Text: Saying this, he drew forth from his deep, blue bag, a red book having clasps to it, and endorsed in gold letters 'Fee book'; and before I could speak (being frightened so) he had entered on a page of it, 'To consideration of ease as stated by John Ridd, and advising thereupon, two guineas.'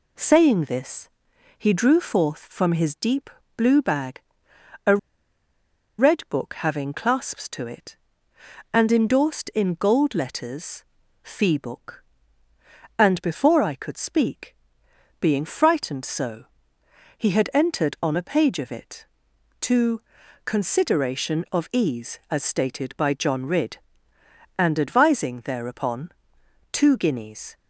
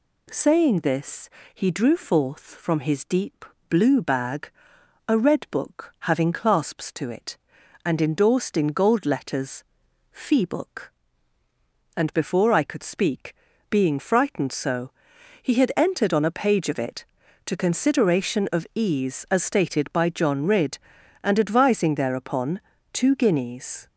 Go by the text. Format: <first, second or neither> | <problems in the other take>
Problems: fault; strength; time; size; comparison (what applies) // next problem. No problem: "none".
second | pauses between "a" and "red"; at 4.9 s; 1.0 s long // pauses between "letters" and "Fee"; at 10.8 s; 0.40 s long; noticeable in the second // pauses between "To" and "consideration"; at 20.0 s; 0.42 s long